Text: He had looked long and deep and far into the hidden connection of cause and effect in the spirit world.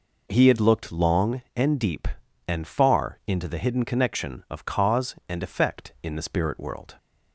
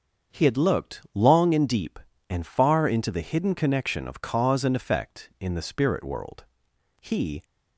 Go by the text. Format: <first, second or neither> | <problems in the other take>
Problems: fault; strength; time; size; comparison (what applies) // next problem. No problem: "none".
first | starts louder than the rest; until 1.4 s; 7 dB // goes on to say "He"; slight; from 7.0 s on; 0.42 s long